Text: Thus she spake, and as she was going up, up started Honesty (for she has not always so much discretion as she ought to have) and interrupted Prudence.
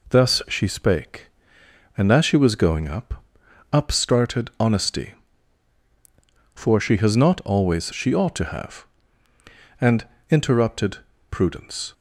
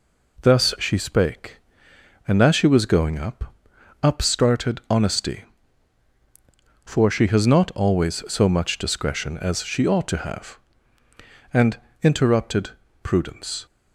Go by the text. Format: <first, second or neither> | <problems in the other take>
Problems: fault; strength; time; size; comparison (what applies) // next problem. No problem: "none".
second | skips "so much discretion as"; at 7.9 s // pauses between "and" and "interrupted"; slight; at 10.0 s; 0.26 s long; slight in the second // pauses between "interrupted" and "Prudence"; slight; at 10.9 s; 0.30 s long; slight in the second